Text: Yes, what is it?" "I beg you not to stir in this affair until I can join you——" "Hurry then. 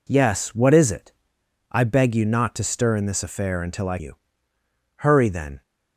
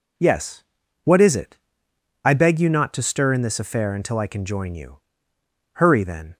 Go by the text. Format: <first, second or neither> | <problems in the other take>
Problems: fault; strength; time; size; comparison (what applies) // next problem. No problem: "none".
second | skips "can join"; at 3.9 s